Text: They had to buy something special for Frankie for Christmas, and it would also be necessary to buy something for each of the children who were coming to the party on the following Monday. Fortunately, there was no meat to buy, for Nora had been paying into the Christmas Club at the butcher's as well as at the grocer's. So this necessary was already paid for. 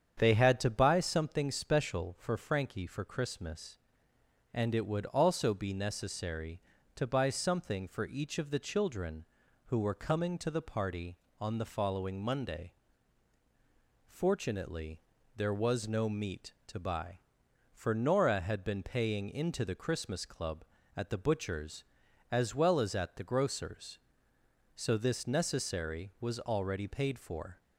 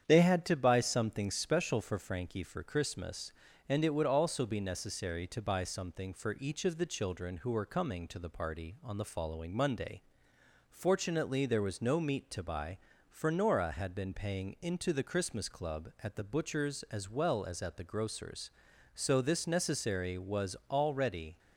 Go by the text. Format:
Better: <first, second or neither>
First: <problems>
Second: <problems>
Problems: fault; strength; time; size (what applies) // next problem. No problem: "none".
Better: first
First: starts louder than the rest; strong; until 1.2 s; 8 dB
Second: starts louder than the rest; strong; until 1.0 s; 8.5 dB // pauses between "was" and "already"; slight; at 20.5 s; 0.16 s long // stops before "paid for"; at 21.3 s